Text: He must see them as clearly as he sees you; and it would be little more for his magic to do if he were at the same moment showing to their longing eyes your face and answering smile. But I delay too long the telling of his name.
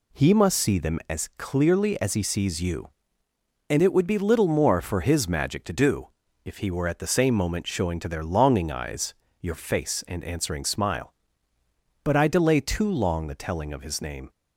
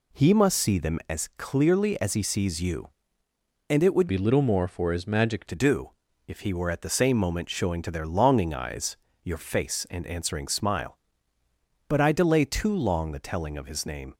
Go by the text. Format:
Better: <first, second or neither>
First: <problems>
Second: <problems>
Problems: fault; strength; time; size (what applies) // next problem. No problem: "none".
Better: first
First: pauses between "do" and "if"; slight; at 6.0 s; 0.36 s long // pauses between "eyes" and "your"; slight; at 9.1 s; 0.28 s long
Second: changes voice from "be" to "magic"; from 4.0 to 5.4 s; 1.4 s long // pauses between "do" and "if"; slight; at 5.9 s; 0.36 s long // pauses between "eyes" and "your"; slight; at 8.9 s; 0.28 s long